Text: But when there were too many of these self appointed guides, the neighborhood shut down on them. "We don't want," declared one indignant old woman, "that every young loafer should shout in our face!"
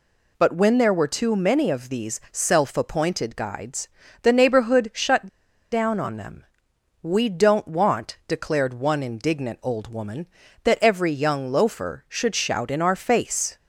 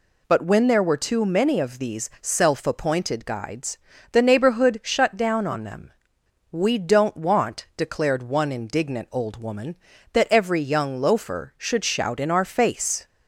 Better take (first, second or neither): second